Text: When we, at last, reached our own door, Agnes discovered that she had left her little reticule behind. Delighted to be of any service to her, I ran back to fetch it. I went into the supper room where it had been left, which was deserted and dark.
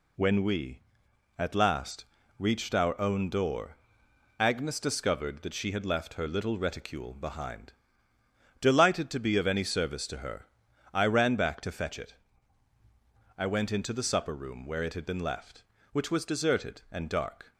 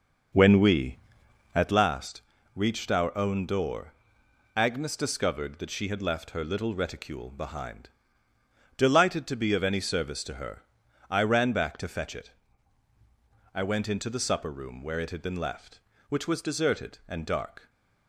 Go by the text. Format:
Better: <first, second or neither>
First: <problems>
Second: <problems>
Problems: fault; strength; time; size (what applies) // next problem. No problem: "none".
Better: first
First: none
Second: starts louder than the rest; until 1.9 s; 6.5 dB // stays silent after the last word; slight; from 17.5 s on; 0.5 s long